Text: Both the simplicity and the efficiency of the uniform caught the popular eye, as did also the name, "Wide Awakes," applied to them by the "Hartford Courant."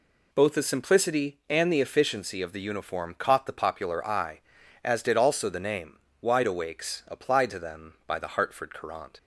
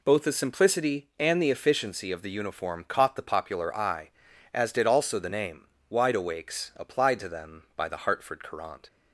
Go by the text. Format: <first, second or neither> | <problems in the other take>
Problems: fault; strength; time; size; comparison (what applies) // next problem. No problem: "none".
neither | none